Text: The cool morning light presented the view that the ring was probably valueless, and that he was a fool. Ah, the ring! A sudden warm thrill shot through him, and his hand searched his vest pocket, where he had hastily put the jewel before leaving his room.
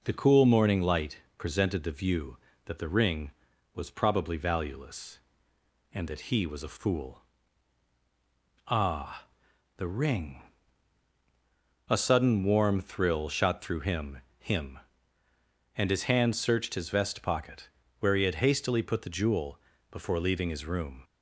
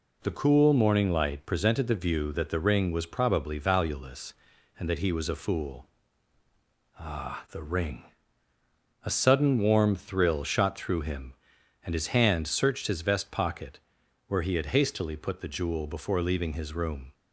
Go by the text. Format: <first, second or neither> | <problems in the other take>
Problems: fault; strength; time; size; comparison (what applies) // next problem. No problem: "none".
second | pauses between "light" and "presented"; slight; at 1.1 s; 0.20 s long // says "him" twice; at 14.3 s // pauses between "jewel" and "before"; slight; at 19.6 s; 0.30 s long